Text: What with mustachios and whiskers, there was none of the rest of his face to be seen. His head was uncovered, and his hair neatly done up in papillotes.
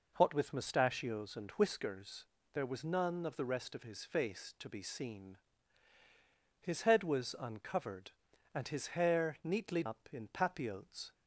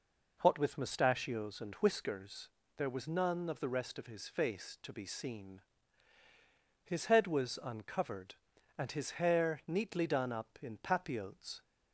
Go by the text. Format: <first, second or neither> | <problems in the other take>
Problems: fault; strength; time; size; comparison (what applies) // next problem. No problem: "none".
second | skips "done"; at 9.8 s